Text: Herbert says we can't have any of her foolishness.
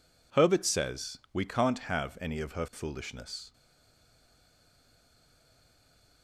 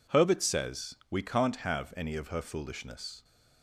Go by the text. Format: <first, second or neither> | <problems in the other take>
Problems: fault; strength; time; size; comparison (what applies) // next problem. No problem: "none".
second | stays silent after the last word; strong; from 3.5 s on; 2.7 s long